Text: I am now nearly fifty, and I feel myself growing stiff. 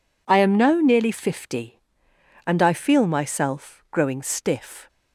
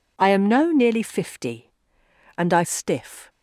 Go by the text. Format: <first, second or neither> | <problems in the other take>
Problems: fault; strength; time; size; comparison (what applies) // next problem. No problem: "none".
first | skips "feel myself growing"; at 2.6 s